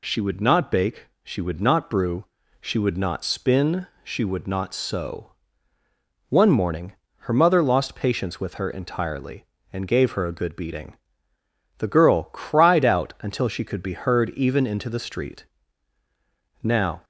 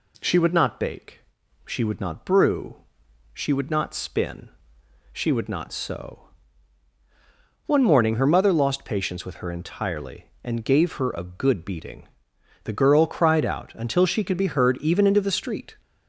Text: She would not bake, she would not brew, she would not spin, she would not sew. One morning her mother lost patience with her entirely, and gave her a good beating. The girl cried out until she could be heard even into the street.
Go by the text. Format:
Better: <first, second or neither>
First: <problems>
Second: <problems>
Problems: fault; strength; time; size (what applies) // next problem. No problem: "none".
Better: second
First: pauses between "morning" and "her"; slight; at 6.9 s; 0.28 s long // goes on to say "Now"; slight; from 16.6 s on; 0.42 s long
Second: none